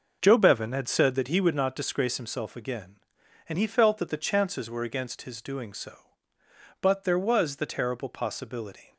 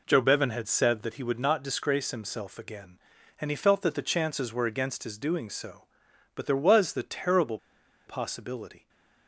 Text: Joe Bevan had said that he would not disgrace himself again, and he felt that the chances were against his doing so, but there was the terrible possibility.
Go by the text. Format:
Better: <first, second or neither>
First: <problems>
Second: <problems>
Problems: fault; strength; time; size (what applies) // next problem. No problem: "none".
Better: first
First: none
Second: pauses between "terrible" and "possibility"; noticeable; at 7.5 s; 0.49 s long